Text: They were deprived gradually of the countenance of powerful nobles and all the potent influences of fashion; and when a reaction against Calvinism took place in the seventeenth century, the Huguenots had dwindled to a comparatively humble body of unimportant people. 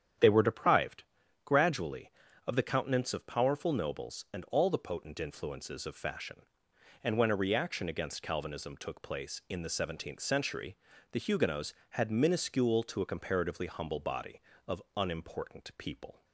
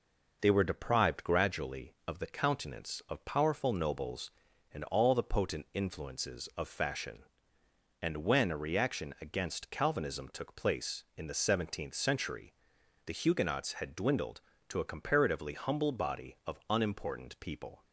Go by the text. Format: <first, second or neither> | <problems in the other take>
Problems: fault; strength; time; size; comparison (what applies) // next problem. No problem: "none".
second | starts louder than the rest; strong; until 1.6 s; 9.5 dB // pauses between "deprived" and "gradually"; at 1.0 s; 0.40 s long // says "minuscule" for "dwindled"; at 12.1 s